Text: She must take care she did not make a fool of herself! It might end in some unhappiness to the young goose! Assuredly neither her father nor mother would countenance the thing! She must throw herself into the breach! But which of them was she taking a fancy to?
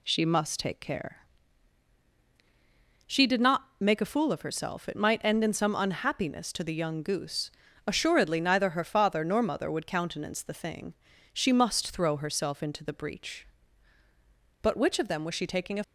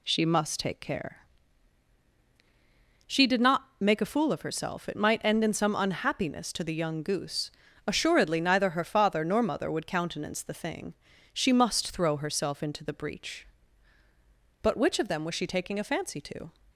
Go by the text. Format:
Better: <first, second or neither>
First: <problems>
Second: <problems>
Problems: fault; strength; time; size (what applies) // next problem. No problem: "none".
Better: second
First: pauses between "care" and "she"; strong; at 1.2 s; 1.8 s long // stops before "fancy to"; at 15.8 s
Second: pauses between "care" and "she"; strong; at 1.2 s; 1.8 s long